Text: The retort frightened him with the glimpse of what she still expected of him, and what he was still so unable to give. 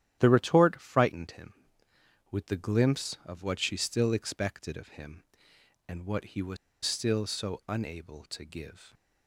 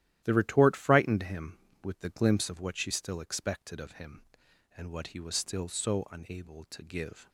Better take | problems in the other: second | starts louder than the rest; strong; until 1.2 s; 11.5 dB; strong in the second // pauses between "was" and "still"; slight; at 6.5 s; 0.28 s long

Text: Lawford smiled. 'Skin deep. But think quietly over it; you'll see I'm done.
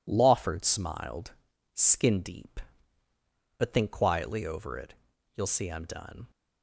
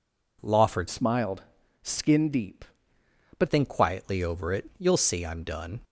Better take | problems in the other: first | changes voice from "smiled" to "But"; from 0.8 to 3.4 s; 2.6 s long

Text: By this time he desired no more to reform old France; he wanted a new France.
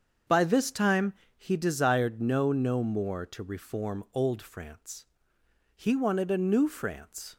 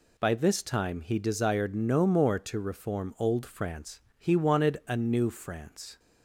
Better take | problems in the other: second | starts louder than the rest; until 1.5 s; 7 dB // pauses between "time" and "he"; slight; at 1.1 s; 0.24 s long // says "no" twice; at 2.5 s

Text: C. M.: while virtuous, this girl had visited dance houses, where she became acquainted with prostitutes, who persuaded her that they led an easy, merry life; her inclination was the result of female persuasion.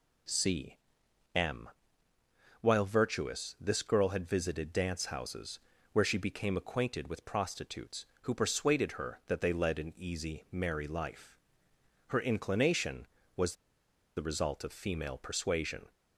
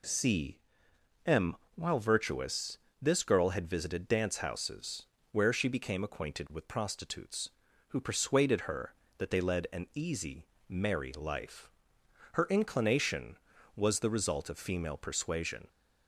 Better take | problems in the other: second | pauses between "was" and "the"; noticeable; at 13.5 s; 0.63 s long

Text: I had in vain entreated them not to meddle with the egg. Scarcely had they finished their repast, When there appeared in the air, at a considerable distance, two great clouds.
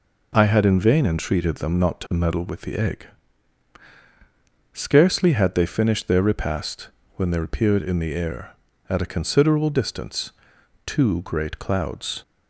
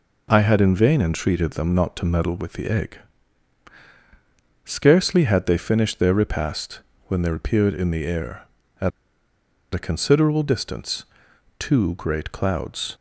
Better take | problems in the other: first | pauses between "at" and "a"; noticeable; at 8.9 s; 0.84 s long

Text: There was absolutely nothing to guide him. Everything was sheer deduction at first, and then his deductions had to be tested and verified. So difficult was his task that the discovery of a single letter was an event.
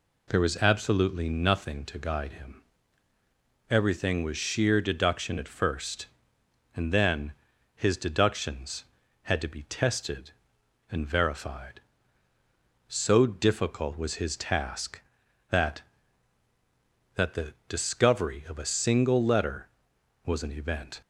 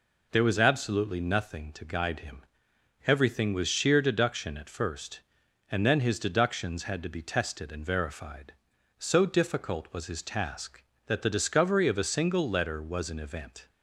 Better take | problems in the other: second | pauses between "then" and "his"; at 7.3 s; 0.42 s long // says "that" twice; at 17.1 s

